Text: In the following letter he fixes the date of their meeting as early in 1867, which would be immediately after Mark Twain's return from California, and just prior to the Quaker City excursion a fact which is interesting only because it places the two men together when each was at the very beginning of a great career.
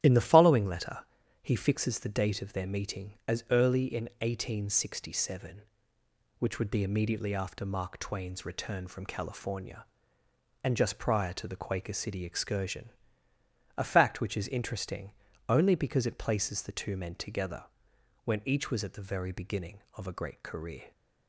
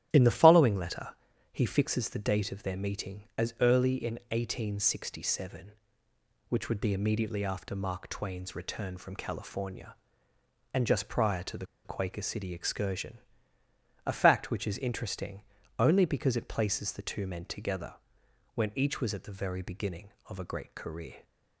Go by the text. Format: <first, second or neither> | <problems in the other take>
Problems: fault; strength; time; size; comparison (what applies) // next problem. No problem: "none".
first | starts louder than the rest; strong; until 1.1 s; 11.5 dB; strong in the first // pauses between "letter" and "he"; at 1.1 s; 0.38 s long; also in the first // pauses between "the" and "Quaker"; slight; at 11.6 s; 0.20 s long // pauses between "excursion" and "a"; noticeable; at 13.1 s; 0.88 s long; noticeable in the first // pauses between "interesting" and "only"; at 15.4 s; 0.38 s long; also in the first // pauses between "together" and "when"; noticeable; at 17.9 s; 0.58 s long; noticeable in the first